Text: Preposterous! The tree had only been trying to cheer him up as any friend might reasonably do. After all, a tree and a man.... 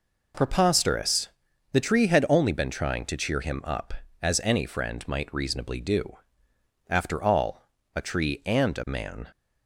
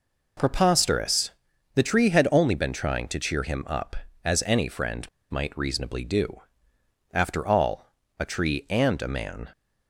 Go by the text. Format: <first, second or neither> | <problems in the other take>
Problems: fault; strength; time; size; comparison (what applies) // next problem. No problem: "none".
first | pauses between "friend" and "might"; slight; at 5.0 s; 0.27 s long